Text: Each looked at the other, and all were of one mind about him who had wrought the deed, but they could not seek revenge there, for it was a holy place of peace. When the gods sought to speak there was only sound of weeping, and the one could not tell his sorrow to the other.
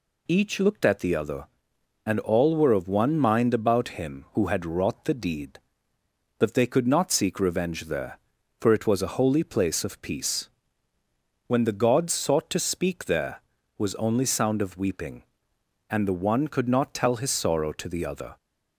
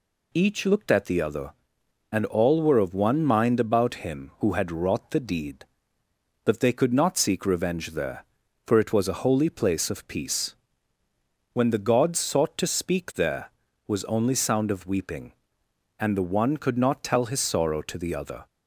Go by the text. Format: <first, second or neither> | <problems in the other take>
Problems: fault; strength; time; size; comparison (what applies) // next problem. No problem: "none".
neither | none